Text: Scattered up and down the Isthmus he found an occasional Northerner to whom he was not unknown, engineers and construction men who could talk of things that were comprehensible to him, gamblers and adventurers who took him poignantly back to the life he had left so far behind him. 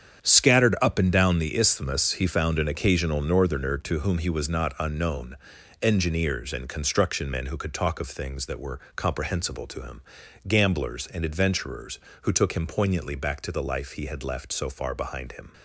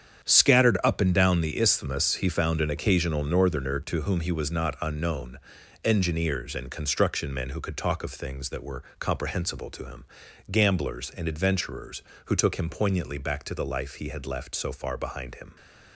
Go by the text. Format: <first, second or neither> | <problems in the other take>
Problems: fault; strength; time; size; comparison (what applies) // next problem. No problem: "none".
neither | starts louder than the rest; strong; the same in both // pauses between "were" and "comprehensible"; slight; the same in both